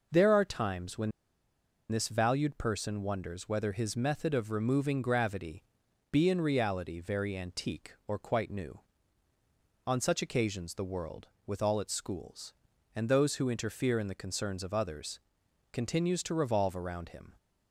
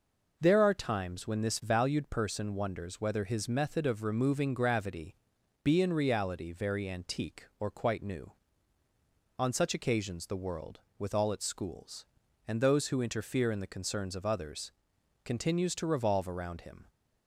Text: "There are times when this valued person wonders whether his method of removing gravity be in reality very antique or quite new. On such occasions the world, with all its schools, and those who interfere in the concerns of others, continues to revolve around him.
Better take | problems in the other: second | pauses between "when" and "this"; noticeable; at 1.1 s; 0.79 s long // pauses between "gravity" and "be"; noticeable; at 5.6 s; 0.48 s long; noticeable in the second

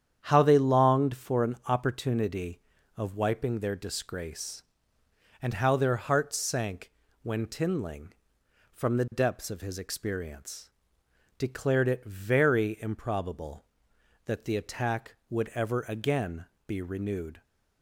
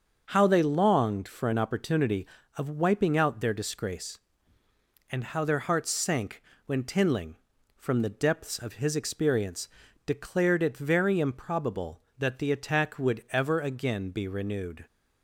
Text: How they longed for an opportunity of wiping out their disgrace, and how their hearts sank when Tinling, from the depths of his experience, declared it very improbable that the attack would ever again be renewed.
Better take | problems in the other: second | starts louder than the rest; strong; until 1.2 s; 9 dB; also in the second // skips "out"; at 3.5 s // pauses between "sank" and "when"; slight; at 6.9 s; 0.32 s long; slight in the second // pauses between "again" and "be"; slight; at 16.4 s; 0.22 s long

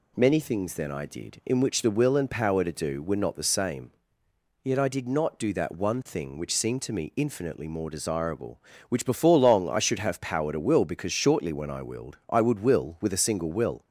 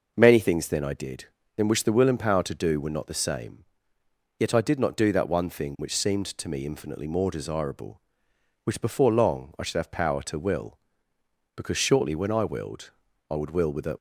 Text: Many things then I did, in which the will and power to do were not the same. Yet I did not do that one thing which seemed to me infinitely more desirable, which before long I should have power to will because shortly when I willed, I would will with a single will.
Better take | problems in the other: first | stops before "single will"; at 13.9 s

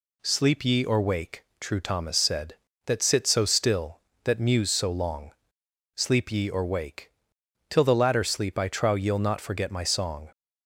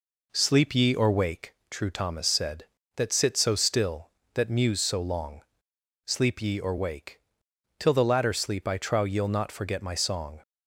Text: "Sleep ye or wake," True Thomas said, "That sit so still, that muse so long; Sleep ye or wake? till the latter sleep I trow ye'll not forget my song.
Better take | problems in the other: first | starts louder than the rest; until 1.4 s; 4 dB

